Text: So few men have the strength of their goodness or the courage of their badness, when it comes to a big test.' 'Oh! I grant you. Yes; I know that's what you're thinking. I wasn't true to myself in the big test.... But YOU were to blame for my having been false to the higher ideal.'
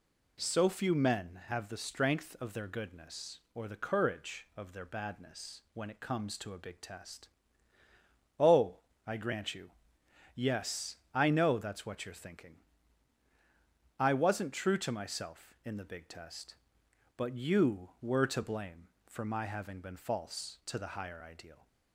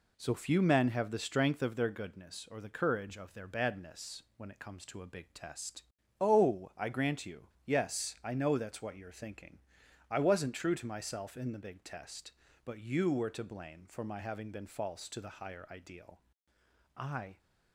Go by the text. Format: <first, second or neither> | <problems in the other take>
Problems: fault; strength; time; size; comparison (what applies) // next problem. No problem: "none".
first | goes on to say "I"; slight; from 16.9 s on; 0.40 s long